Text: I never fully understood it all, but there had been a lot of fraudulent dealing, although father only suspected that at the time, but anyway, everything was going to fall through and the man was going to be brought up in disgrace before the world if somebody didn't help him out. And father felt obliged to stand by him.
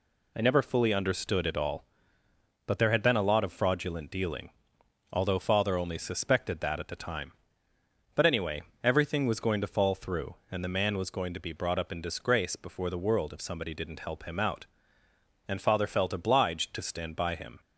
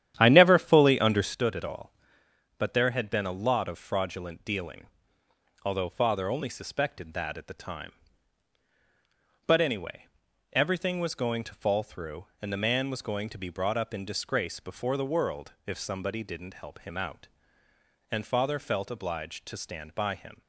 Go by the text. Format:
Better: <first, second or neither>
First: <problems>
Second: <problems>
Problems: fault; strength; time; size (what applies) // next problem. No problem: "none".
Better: first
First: none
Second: starts louder than the rest; strong; until 1.4 s; 11 dB // pauses between "world" and "if"; slight; at 15.5 s; 0.16 s long